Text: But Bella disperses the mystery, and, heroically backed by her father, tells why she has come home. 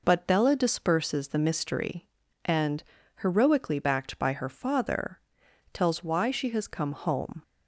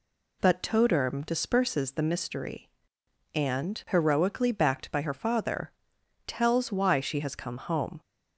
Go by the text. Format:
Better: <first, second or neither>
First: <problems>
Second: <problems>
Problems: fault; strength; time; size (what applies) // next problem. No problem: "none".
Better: first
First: none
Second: says "Toderm" for "Bella"; at 0.6 s